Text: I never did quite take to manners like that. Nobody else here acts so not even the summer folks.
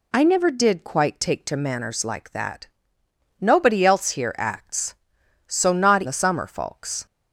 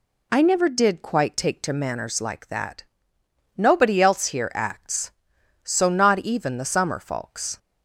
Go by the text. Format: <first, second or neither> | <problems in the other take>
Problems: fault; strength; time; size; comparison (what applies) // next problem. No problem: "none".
second | skips "even"; at 6.0 s